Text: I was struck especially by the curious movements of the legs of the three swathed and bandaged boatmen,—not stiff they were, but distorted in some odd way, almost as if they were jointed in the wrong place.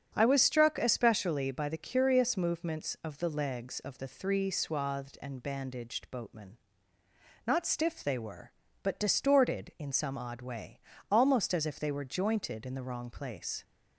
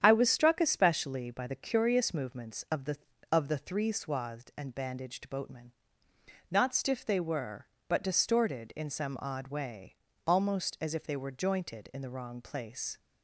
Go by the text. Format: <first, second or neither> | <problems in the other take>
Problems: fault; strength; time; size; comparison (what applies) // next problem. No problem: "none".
first | starts louder than the rest; strong; until 1.0 s; 9 dB; strong in the first // skips "legs"; at 3.1 s